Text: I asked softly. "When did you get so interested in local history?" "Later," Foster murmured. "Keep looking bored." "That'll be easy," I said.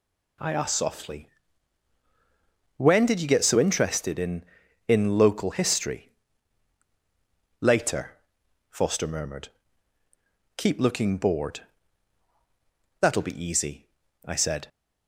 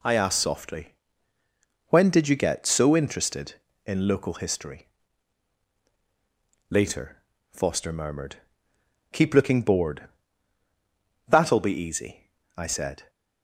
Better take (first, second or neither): second